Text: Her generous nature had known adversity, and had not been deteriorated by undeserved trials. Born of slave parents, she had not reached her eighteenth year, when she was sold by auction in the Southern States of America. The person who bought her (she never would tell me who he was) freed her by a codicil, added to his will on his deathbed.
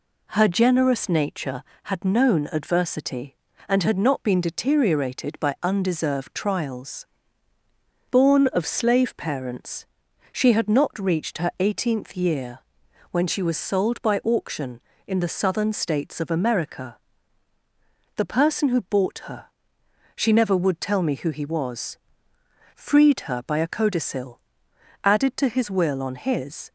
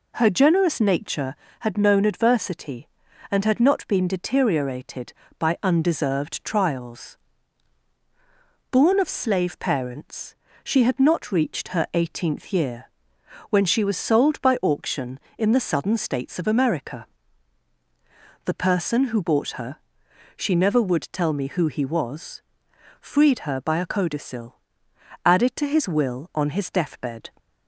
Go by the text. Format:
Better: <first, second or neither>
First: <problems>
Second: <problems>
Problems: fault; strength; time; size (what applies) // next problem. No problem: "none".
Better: second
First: stops before "deathbed"; at 26.6 s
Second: none